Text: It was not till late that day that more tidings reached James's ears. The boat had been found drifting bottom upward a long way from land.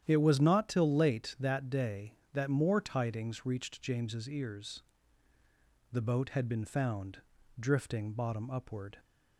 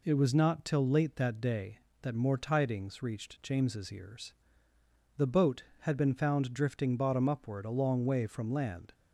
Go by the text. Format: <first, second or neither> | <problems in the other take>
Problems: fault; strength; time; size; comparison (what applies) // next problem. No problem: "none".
second | starts louder than the rest; strong; until 1.0 s; 10 dB // pauses between "found" and "drifting"; at 7.2 s; 0.38 s long // stops before "a long way from land"; at 8.9 s